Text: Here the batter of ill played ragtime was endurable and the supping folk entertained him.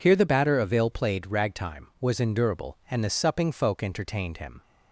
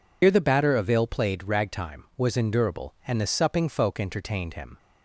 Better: first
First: none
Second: loses the start of "Here"; at 0.2 s; 70 ms

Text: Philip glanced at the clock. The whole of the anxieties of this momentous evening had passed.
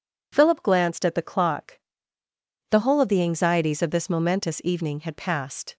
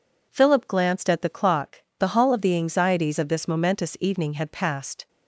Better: first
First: none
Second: says "hall" for "whole"; at 2.0 s

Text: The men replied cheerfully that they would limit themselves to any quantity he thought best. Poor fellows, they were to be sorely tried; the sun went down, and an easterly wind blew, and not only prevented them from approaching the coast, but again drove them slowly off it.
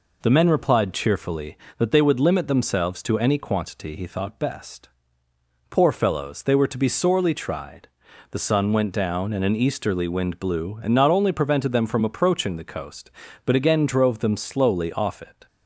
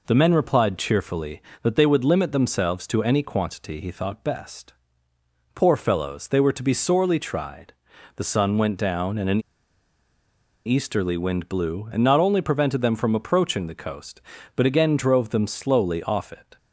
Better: first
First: none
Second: pauses between "an" and "easterly"; strong; at 9.4 s; 1.2 s long

